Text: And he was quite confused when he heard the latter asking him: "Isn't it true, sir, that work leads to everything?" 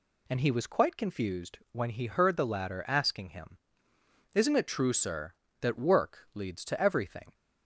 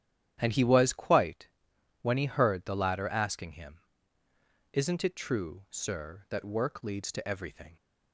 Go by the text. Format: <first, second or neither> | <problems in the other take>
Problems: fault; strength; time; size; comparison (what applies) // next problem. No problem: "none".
first | starts louder than the rest; strong; until 1.4 s; 11 dB // skips "confused"; at 1.7 s